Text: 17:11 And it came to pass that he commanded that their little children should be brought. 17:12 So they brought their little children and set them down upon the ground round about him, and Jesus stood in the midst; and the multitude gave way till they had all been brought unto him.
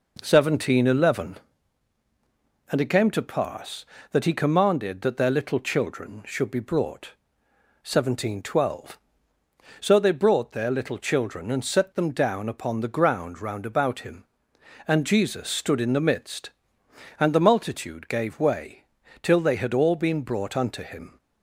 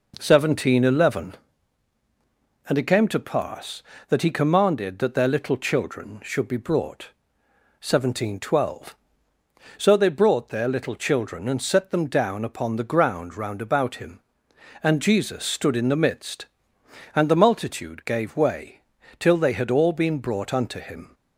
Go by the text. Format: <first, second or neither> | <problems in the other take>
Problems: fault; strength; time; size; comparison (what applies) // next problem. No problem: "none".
neither | pauses between "way" and "till"; the same in both